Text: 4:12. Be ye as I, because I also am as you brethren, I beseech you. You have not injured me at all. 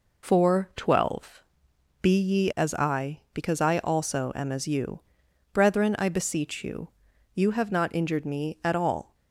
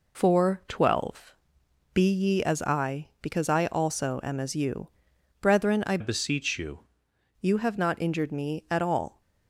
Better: first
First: pauses between "you" and "brethren"; noticeable; at 4.9 s; 0.54 s long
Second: pauses between "you" and "brethren"; noticeable; at 4.8 s; 0.54 s long // changes voice from "beseech" to "you"; from 6.0 to 6.8 s; 0.8 s long

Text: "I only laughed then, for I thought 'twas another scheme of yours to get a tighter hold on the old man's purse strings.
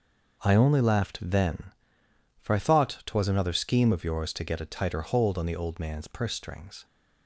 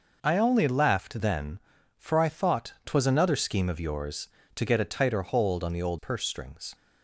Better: first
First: none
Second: skips "man's"; at 5.9 s

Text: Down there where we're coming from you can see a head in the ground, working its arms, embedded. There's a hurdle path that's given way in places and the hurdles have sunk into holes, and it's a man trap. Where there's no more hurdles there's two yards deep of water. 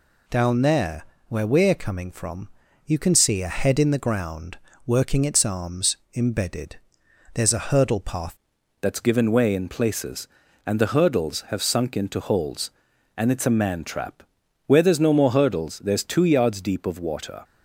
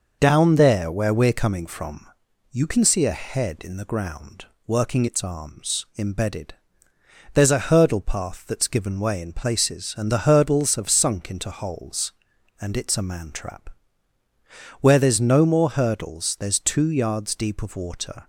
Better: second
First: pauses between "there" and "where"; slight; at 1.0 s; 0.24 s long // pauses between "from" and "you"; slight; at 2.4 s; 0.36 s long // changes voice at "that's"; from 8.8 s on; 8.6 s long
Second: pauses between "from" and "you"; at 2.0 s; 0.44 s long

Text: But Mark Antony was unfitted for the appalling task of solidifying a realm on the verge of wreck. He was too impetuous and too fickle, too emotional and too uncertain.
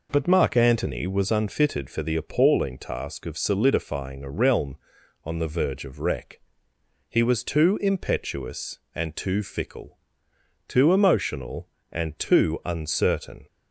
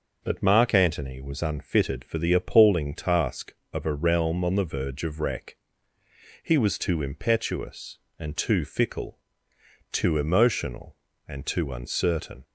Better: first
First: none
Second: skips "solidifying"; at 3.8 s

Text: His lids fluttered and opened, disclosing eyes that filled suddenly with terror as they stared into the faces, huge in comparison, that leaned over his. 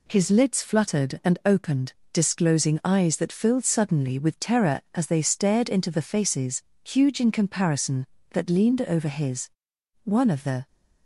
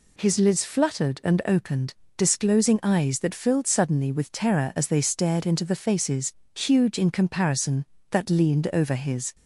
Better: second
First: goes on to say "One of the"; noticeable; from 10.0 s on; 0.62 s long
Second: none

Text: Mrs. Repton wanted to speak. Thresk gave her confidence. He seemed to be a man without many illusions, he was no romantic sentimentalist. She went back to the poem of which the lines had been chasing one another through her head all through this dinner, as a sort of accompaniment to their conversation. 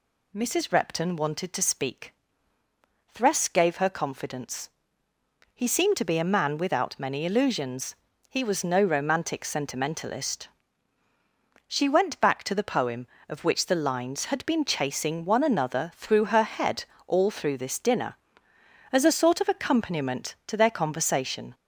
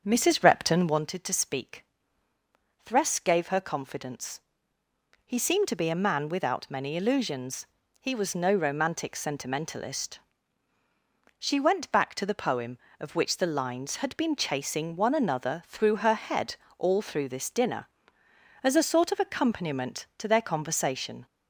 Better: first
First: pauses between "head" and "all"; slight; at 16.8 s; 0.20 s long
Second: starts louder than the rest; until 1.0 s; 7 dB // pauses between "head" and "all"; slight; at 16.5 s; 0.20 s long

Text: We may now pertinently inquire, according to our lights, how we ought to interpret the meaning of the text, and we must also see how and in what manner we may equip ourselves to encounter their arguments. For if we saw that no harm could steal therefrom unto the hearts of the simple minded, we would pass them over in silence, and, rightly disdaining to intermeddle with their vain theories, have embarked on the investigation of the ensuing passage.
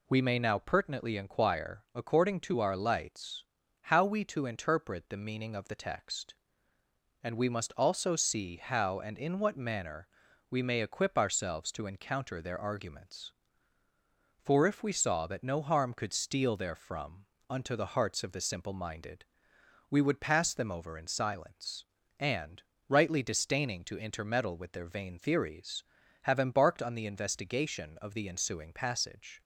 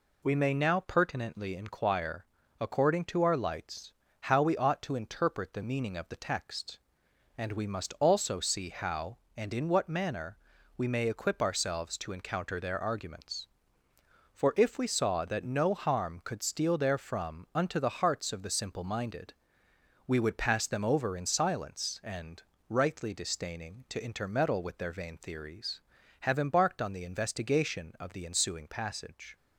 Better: second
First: skips "ought"; at 4.2 s // pauses between "manner" and "we"; at 10.0 s; 0.44 s long // pauses between "therefrom" and "unto"; slight; at 17.2 s; 0.24 s long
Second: pauses between "manner" and "we"; at 10.3 s; 0.40 s long

